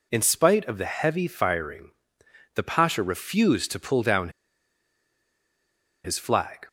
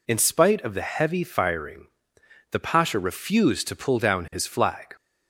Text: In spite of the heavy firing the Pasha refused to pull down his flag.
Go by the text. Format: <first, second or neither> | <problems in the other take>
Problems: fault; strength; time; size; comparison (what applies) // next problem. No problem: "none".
second | pauses between "firing" and "the"; noticeable; at 1.9 s; 0.62 s long; noticeable in the second // pauses between "down" and "his"; strong; at 4.2 s; 1.7 s long